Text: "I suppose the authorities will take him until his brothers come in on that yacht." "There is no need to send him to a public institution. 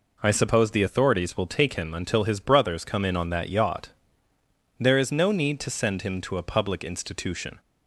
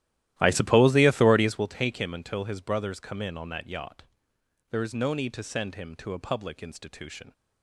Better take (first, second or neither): first